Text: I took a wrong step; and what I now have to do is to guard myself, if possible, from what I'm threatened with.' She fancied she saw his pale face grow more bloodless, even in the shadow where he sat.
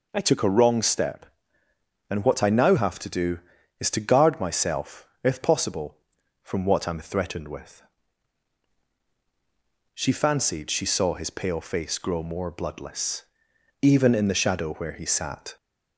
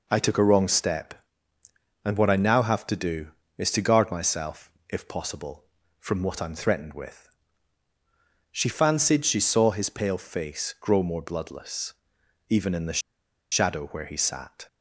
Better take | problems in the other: first | pauses between "the" and "shadow"; noticeable; at 13.0 s; 0.50 s long

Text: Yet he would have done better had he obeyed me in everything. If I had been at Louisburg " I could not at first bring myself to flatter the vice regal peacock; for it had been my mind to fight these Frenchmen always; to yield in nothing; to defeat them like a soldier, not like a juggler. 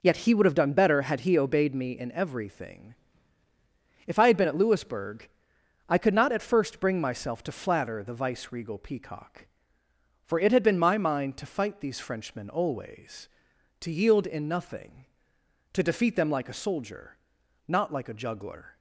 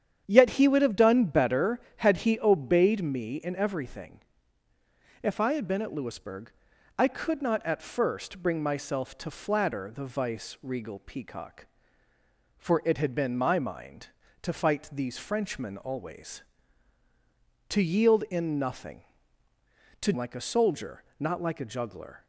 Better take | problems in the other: first | starts louder than the rest; strong; until 1.2 s; 9 dB // skips "defeat them"; at 20.1 s

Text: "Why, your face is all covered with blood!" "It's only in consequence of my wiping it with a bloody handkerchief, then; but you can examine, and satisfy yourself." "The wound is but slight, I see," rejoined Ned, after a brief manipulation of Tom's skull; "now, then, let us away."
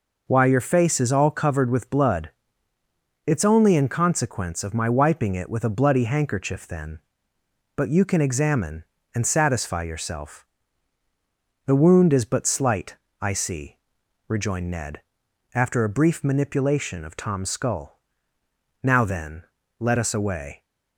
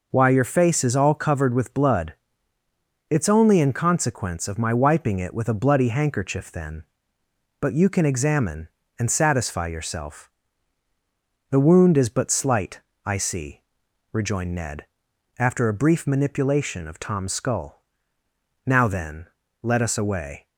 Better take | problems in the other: neither | none

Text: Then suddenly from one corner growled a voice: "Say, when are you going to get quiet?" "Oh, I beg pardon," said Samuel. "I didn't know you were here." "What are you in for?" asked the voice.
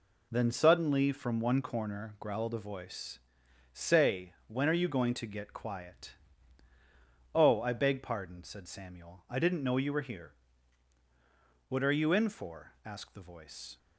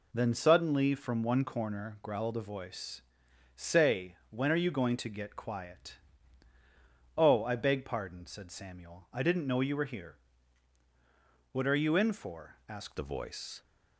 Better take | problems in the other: first | changes voice at "the"; from 12.9 s on; 0.7 s long

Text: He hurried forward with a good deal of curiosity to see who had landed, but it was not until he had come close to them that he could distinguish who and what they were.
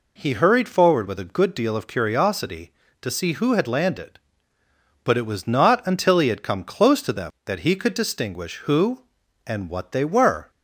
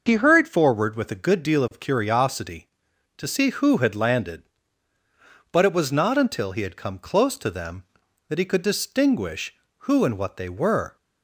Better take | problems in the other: neither | none

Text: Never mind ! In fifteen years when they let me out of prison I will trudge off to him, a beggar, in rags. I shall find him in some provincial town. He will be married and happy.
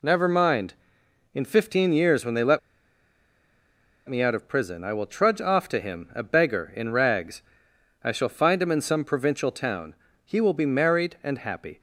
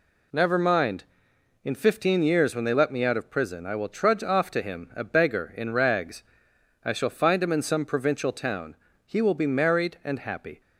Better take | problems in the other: second | pauses between "let" and "me"; strong; at 2.5 s; 1.4 s long

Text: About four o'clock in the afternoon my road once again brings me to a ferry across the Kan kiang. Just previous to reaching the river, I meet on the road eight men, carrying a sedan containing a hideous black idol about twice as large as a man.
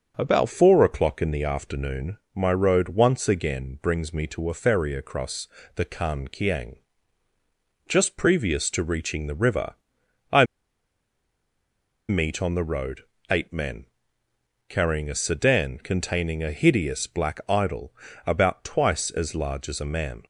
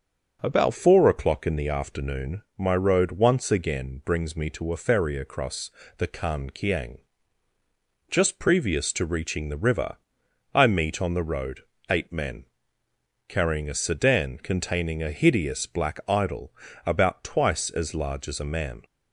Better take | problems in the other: second | pauses between "afternoon" and "my"; slight; at 2.1 s; 0.16 s long // pauses between "across" and "the"; slight; at 5.4 s; 0.28 s long; slight in the second // pauses between "I" and "meet"; strong; at 10.4 s; 1.6 s long // pauses between "road" and "eight"; slight; at 13.0 s; 0.28 s long; slight in the second // pauses between "idol" and "about"; slight; at 17.9 s; 0.34 s long; slight in the second

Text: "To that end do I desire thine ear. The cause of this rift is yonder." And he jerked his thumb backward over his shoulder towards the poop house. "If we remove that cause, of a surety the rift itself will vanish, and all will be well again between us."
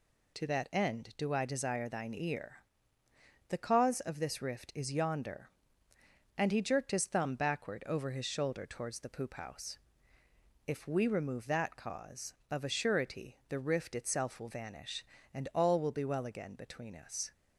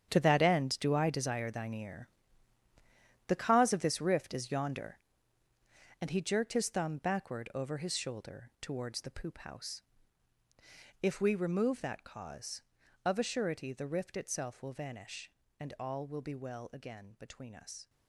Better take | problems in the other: first | gets quieter; strong; throughout; 12.5 dB

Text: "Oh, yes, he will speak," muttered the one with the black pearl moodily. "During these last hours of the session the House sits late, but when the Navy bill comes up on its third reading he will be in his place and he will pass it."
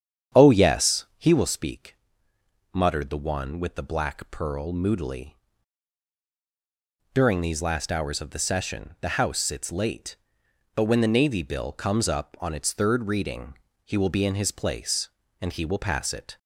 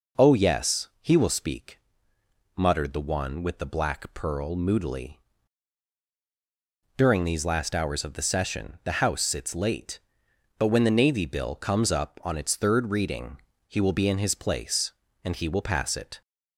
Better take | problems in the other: second | starts louder than the rest; strong; until 1.4 s; 8.5 dB // pauses between "reading" and "he"; slight; at 13.5 s; 0.26 s long; slight in the second

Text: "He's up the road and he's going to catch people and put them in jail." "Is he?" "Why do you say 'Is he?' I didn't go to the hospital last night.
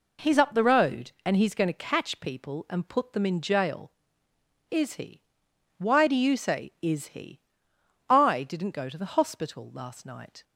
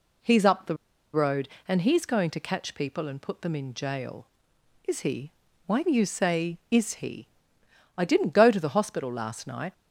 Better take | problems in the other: first | pauses between "the" and "road"; at 0.7 s; 0.38 s long

